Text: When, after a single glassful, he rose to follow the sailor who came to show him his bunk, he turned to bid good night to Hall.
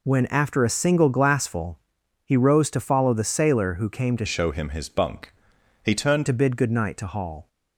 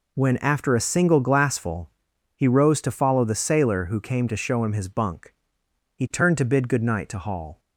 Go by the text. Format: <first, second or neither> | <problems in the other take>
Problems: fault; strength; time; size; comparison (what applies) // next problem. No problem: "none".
second | changes voice from "show" to "turned"; from 4.2 to 6.2 s; 2.0 s long